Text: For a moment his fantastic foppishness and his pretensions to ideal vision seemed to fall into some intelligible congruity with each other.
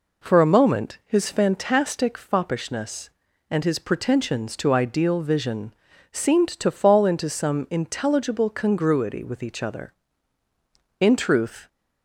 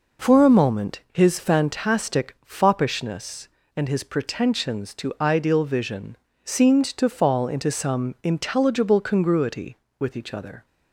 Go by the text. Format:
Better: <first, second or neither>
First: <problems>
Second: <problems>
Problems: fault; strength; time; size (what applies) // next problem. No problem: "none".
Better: second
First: pauses between "vision" and "seemed"; at 5.7 s; 0.38 s long // goes on to say "In truth"; noticeable; from 10.9 s on; 0.68 s long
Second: pauses between "vision" and "seemed"; slight; at 6.1 s; 0.30 s long